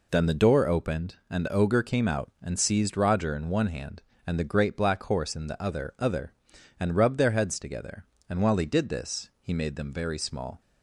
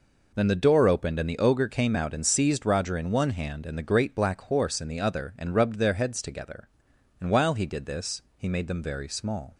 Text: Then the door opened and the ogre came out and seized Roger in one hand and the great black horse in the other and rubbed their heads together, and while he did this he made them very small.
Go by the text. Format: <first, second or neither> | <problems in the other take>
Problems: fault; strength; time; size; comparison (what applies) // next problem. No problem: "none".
second | says "other" twice; at 5.9 s